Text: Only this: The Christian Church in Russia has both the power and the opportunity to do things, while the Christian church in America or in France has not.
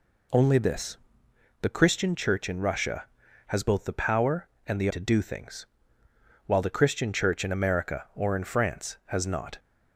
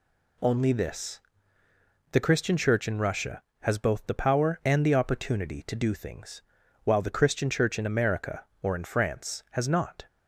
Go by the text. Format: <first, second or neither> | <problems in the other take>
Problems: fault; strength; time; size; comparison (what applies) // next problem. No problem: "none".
second | skips "opportunity"; at 4.9 s